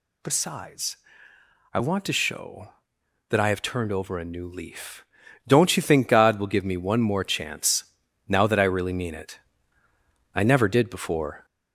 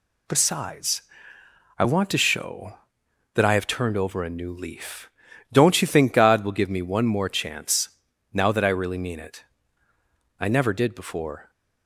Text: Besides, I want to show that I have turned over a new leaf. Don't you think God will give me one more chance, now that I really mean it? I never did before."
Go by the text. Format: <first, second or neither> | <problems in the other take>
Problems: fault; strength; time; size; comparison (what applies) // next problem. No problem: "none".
second | gets louder; slight; throughout; 3.5 dB